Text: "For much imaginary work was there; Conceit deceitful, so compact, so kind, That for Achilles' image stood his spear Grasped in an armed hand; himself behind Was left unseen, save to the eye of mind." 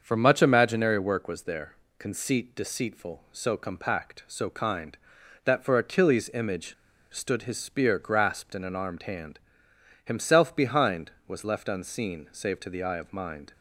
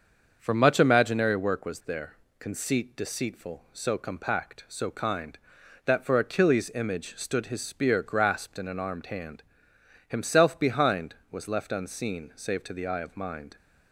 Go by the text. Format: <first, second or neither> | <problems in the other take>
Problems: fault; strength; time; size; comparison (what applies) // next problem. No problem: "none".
second | starts louder than the rest; until 1.0 s; 6.5 dB; also in the second // pauses between "image" and "stood"; at 6.7 s; 0.38 s long